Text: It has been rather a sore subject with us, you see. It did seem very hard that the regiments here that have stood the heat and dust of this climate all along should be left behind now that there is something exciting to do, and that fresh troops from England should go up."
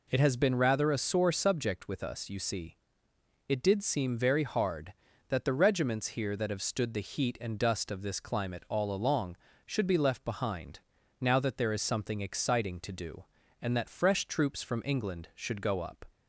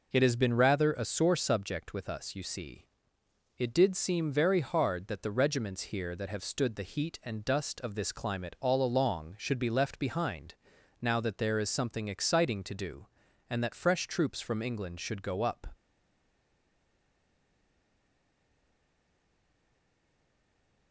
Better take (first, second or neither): first